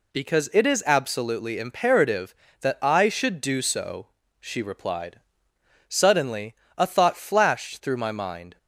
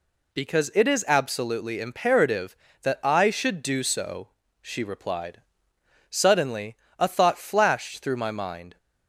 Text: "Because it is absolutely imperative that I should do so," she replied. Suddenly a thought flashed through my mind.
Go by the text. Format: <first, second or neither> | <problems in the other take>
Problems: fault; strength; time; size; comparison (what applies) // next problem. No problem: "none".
neither | pauses between "Suddenly" and "a"; slight; the same in both